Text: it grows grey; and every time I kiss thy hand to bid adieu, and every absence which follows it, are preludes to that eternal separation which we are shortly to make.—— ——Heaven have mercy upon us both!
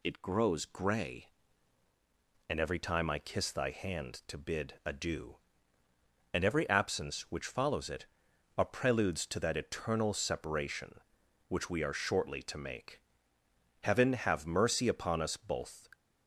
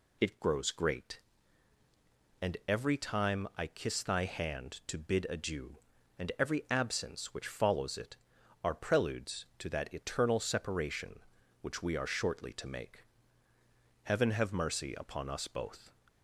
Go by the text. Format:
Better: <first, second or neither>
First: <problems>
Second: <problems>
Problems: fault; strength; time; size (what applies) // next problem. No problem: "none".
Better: first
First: none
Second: says "great" for "grey"; at 0.7 s